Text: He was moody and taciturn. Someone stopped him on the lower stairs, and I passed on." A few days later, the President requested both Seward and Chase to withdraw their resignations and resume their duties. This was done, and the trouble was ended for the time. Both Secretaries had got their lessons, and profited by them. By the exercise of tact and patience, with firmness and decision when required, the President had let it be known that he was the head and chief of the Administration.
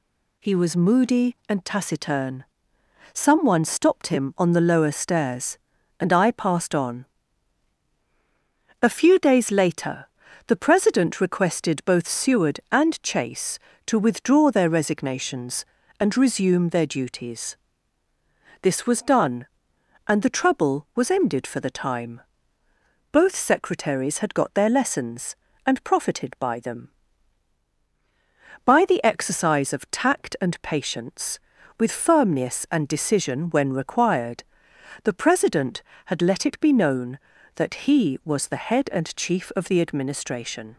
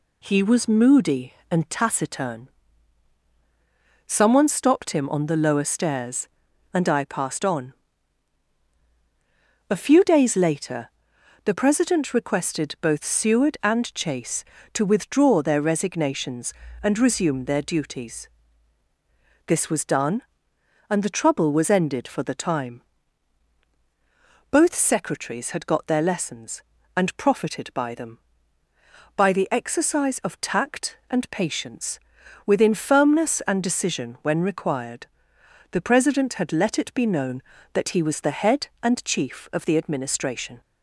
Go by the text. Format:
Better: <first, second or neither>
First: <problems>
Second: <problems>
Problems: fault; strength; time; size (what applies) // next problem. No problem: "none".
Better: first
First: none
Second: says "within" for "with"; at 32.4 s